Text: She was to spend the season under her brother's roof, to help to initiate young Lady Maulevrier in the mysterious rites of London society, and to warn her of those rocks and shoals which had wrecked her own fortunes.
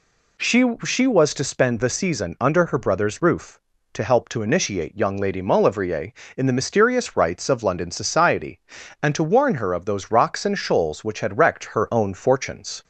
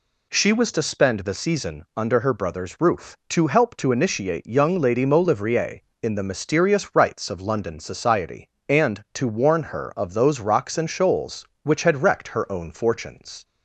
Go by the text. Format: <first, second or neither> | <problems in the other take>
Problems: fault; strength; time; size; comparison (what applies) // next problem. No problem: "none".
second | says "She" twice; at 0.8 s